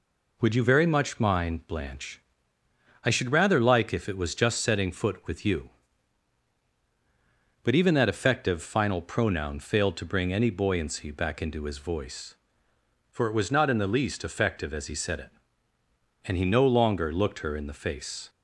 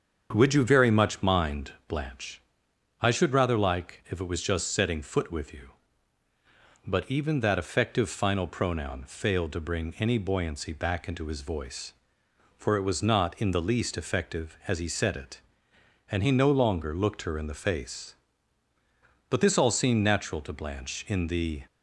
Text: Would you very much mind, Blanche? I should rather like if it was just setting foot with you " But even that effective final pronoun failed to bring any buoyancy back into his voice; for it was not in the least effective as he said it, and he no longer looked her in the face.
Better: first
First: none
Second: starts louder than the rest; strong; until 1.3 s; 7.5 dB // goes on to say "But this all seemed natural to Blanche in the"; strong; from 19.2 s on; 2.3 s long

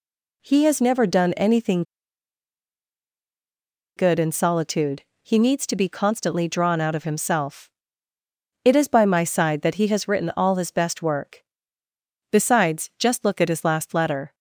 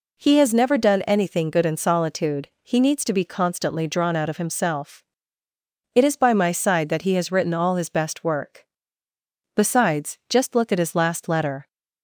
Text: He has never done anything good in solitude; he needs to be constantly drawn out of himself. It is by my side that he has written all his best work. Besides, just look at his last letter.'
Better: second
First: pauses between "anything" and "good"; strong; at 1.8 s; 2.1 s long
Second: none

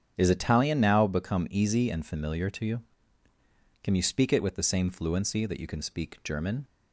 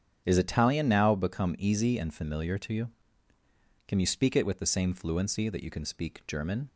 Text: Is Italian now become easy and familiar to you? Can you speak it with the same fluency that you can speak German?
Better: neither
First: starts louder than the rest; strong; until 1.1 s; 8.5 dB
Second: starts louder than the rest; strong; until 1.2 s; 8.5 dB

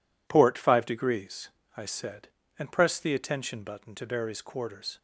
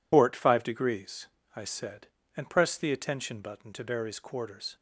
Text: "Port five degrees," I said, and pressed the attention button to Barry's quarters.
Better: first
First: none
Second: loses the start of "Port"; at 0.1 s; 60 ms

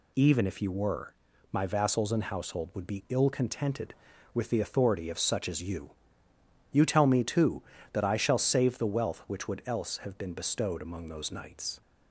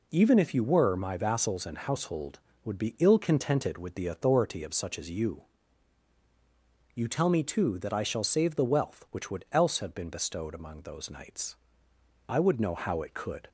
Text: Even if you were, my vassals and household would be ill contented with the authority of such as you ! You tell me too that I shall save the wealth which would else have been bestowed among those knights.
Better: first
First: none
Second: goes on to say "I would know how it could"; noticeable; from 12.2 s on; 1.2 s long

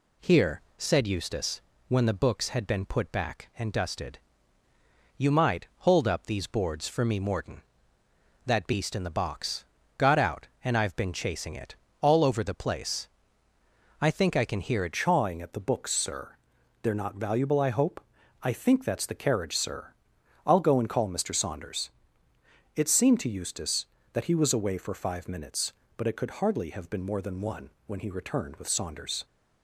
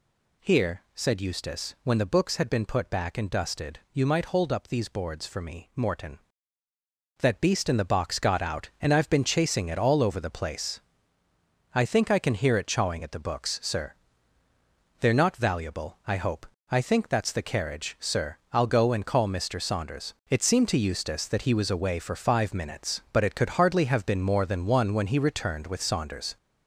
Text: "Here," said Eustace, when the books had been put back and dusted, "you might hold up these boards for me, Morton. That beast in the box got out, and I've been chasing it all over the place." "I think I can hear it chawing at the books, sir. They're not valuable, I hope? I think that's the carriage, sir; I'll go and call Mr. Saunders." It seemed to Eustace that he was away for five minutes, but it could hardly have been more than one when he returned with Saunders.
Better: second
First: pauses between "box" and "got"; slight; at 9.6 s; 0.32 s long // pauses between "it" and "all"; slight; at 11.7 s; 0.26 s long // changes voice at "chawing"; from 14.9 s on; 14.3 s long // pauses between "one" and "when"; slight; at 27.7 s; 0.16 s long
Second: none

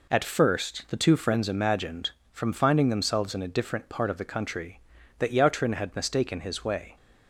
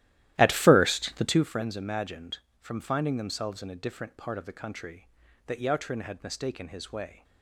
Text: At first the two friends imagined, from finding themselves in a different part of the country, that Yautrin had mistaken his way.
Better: first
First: none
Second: starts louder than the rest; strong; until 1.5 s; 14 dB

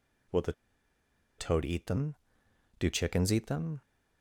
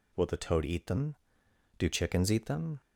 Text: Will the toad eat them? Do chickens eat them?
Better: second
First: pauses between "the" and "toad"; noticeable; at 0.5 s; 0.86 s long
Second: none

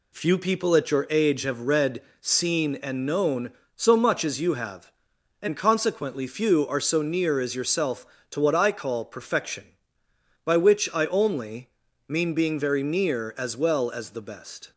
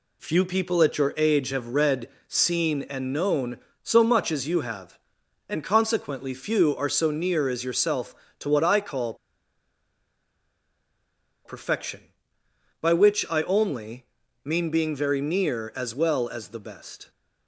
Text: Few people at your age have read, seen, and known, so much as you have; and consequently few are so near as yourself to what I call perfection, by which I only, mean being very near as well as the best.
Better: first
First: none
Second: pauses between "call" and "perfection"; strong; at 9.1 s; 2.3 s long

